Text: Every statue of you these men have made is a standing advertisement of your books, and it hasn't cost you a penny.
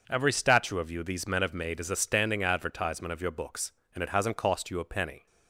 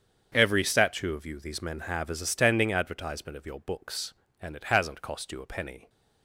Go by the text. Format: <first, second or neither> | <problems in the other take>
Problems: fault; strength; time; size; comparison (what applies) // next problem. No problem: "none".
first | starts louder than the rest; strong; until 1.3 s; 7.5 dB // skips "made"; at 2.0 s